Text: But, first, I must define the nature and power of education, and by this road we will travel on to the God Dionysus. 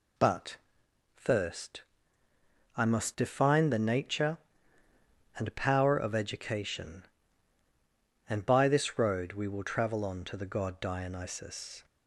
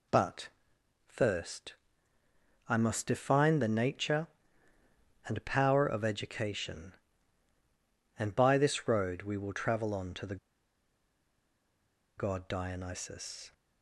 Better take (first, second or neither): first